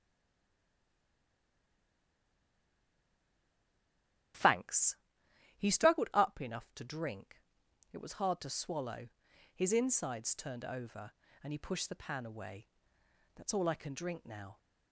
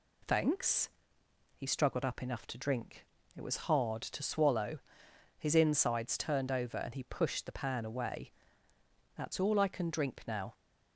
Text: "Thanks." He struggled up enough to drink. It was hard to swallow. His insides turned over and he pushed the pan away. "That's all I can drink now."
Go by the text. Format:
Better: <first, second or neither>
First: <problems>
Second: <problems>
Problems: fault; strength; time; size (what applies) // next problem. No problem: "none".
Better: second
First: stays silent before the first word; strong; until 4.3 s; 4.3 s long // starts louder than the rest; strong; until 5.9 s; 11 dB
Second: none